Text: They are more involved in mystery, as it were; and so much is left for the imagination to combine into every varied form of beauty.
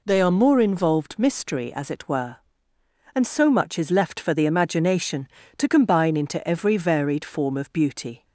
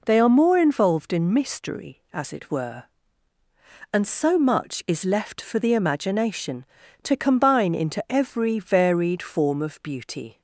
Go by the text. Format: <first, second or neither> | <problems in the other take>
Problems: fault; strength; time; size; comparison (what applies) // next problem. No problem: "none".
second | skips "in"; at 1.1 s